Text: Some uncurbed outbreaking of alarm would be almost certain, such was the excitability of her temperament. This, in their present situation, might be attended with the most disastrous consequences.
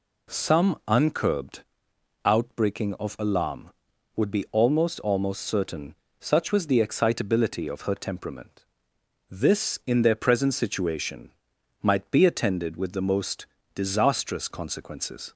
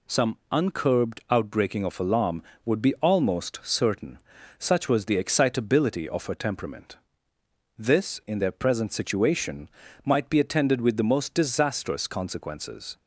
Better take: second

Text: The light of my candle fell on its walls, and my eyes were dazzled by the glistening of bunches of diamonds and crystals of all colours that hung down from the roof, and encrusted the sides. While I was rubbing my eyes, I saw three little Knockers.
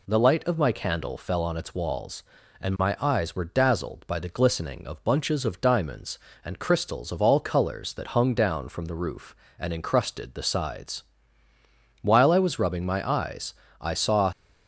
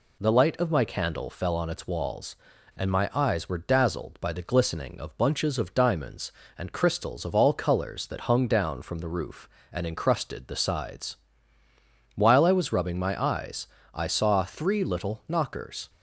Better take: second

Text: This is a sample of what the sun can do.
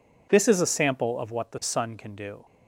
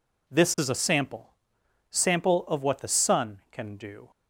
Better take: first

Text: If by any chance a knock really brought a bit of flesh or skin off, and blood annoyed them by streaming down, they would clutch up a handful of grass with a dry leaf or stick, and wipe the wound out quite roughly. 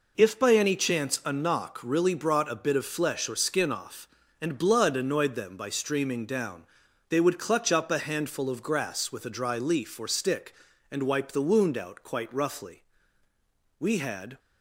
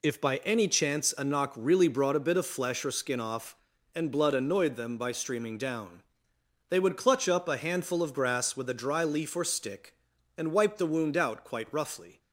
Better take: second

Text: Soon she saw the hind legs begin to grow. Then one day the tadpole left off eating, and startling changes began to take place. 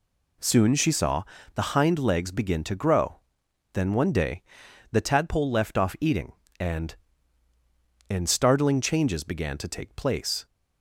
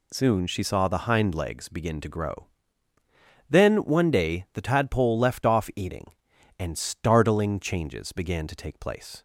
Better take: second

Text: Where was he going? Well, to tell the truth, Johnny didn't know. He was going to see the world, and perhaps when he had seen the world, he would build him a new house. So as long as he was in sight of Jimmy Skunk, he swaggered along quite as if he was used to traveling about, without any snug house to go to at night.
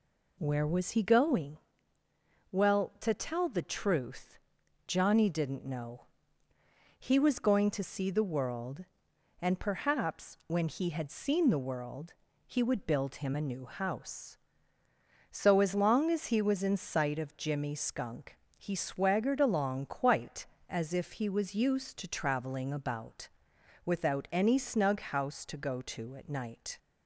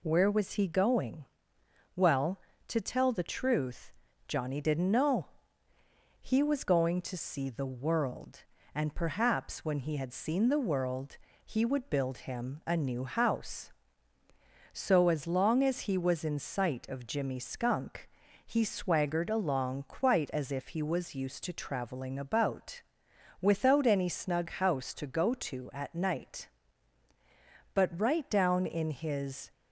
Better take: first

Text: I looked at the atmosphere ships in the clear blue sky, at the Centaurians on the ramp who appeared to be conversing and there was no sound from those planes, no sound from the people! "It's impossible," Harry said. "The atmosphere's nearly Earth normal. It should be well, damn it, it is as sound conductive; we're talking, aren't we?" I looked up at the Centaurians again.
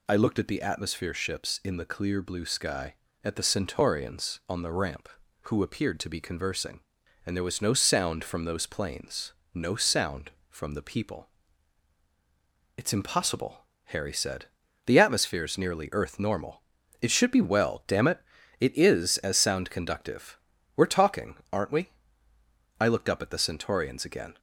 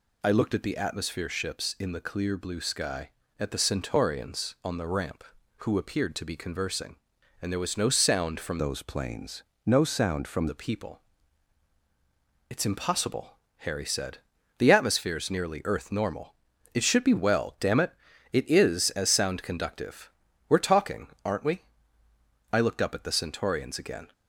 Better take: first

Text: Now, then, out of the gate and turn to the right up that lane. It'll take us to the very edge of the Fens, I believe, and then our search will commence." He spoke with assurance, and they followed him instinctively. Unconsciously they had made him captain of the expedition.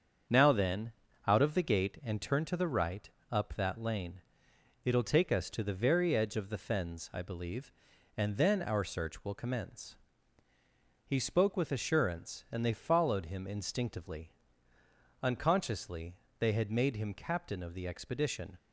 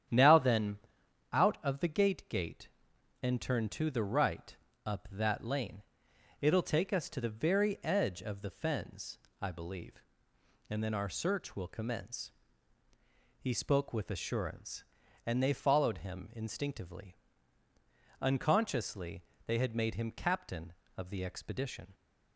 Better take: first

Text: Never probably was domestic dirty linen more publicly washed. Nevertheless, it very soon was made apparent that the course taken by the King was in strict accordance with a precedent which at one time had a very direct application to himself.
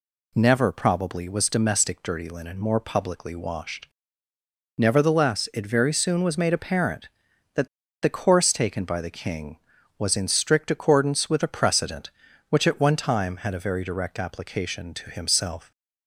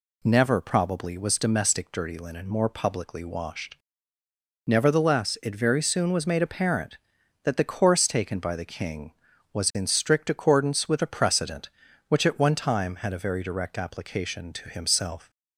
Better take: second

